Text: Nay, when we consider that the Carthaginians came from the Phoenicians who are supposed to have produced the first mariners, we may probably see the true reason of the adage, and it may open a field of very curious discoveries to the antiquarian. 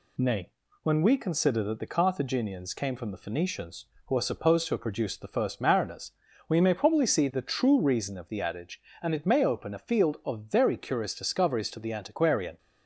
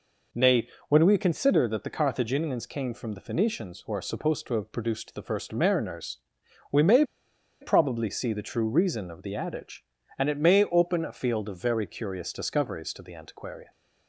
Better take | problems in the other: first | pauses between "may" and "probably"; noticeable; at 7.0 s; 0.58 s long

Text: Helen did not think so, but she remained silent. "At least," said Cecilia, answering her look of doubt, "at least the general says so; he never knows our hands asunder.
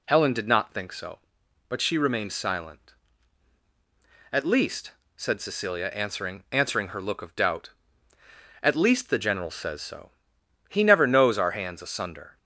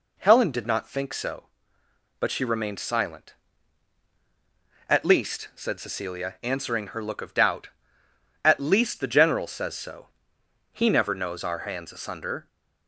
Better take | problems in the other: second | says "answering" twice; at 6.5 s

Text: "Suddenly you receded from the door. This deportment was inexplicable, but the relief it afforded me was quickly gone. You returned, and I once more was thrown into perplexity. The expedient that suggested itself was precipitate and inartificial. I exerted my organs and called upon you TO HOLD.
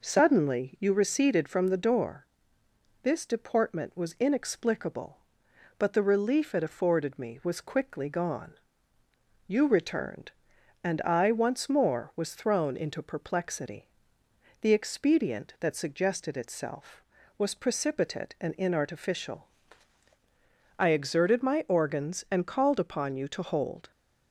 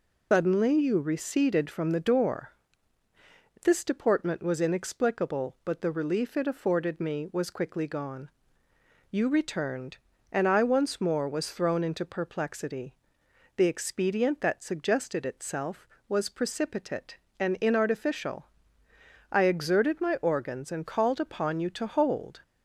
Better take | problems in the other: first | loses the start of "Suddenly"; at 0.3 s; 165 ms

